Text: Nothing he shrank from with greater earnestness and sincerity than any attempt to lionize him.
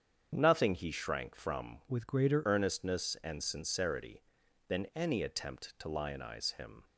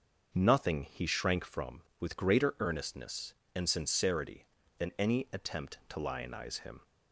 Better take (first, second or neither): second